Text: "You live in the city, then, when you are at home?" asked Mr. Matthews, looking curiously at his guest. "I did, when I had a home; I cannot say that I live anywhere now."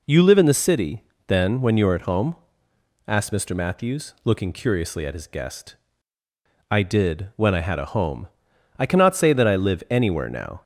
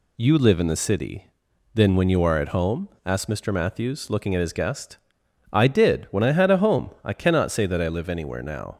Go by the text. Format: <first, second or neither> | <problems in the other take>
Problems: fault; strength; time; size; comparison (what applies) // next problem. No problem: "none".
first | skips "curiously"; at 4.3 s